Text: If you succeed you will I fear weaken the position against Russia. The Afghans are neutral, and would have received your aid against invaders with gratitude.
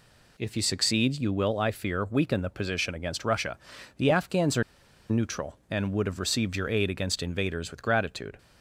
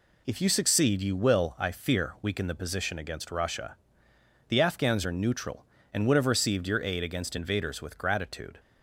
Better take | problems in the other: second | pauses between "are" and "neutral"; noticeable; at 4.6 s; 0.46 s long

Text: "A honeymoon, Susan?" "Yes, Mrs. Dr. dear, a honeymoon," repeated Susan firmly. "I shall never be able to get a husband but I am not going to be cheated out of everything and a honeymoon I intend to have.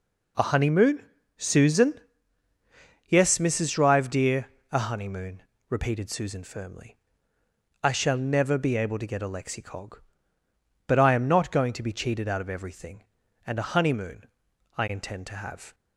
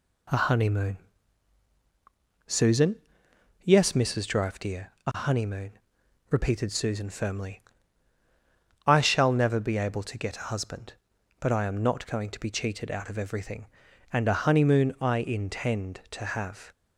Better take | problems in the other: second | says "lexicog" for "husband"; at 9.2 s // pauses between "honeymoon" and "I"; noticeable; at 14.2 s; 0.50 s long

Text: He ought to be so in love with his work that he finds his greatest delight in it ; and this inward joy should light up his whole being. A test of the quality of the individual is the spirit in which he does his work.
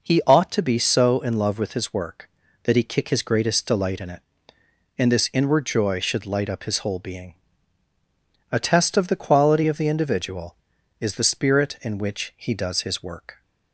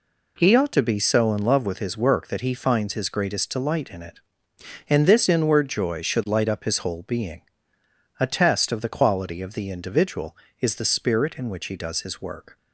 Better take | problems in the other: second | says "kick" for "finds"; at 2.8 s

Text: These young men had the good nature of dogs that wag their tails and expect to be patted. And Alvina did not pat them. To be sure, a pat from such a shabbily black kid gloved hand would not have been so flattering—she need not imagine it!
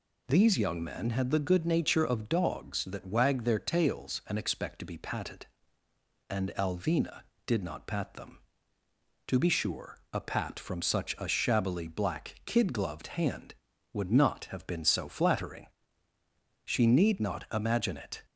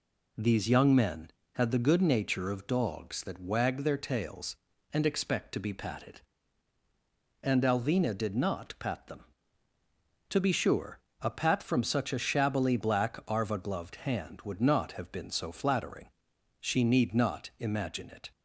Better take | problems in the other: first | says "arva" for "kid"; at 13.2 s

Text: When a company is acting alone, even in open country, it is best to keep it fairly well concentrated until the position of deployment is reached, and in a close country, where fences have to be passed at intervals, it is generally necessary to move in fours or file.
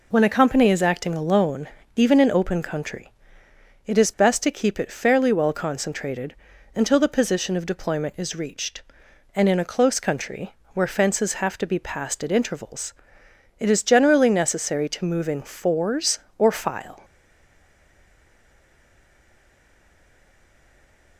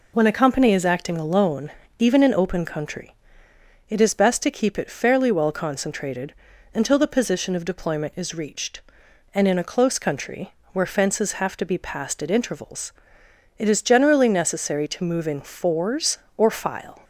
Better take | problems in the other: second | pauses between "concentrated" and "until"; slight; at 6.3 s; 0.36 s long; slight in the second // stays silent after the last word; strong; from 17.0 s on; 4.1 s long

